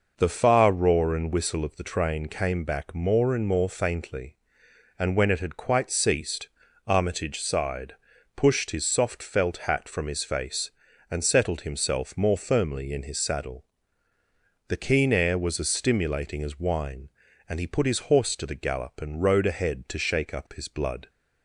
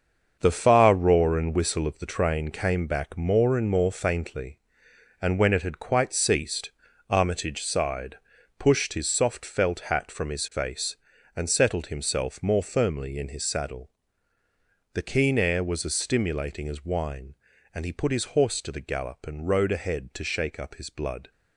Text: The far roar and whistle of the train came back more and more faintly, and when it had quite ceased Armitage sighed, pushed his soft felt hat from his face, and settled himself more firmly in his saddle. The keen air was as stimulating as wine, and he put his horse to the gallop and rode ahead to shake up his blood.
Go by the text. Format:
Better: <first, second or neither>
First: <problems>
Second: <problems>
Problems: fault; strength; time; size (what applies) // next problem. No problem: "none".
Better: first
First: pauses between "ceased" and "Armitage"; slight; at 6.4 s; 0.36 s long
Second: gets quieter; strong; throughout; 9 dB // pauses between "ceased" and "Armitage"; slight; at 6.7 s; 0.36 s long